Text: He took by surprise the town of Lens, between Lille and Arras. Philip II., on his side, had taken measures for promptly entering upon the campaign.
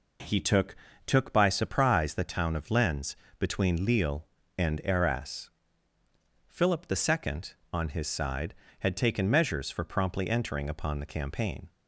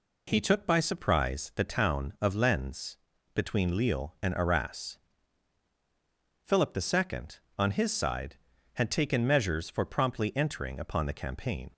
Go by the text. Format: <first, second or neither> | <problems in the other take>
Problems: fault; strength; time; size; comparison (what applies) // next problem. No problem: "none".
second | says "took" twice; at 1.0 s